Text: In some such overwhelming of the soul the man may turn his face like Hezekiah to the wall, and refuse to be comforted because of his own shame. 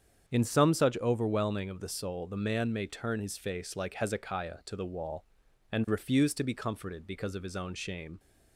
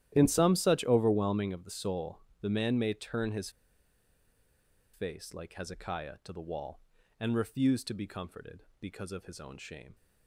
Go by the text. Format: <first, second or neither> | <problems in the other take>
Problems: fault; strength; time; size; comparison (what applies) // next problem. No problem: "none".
first | starts louder than the rest; strong; until 1.1 s; 12.5 dB; strong in the first // pauses between "soul" and "the"; slight; at 2.2 s; 0.20 s long // pauses between "his" and "face"; strong; at 3.4 s; 1.4 s long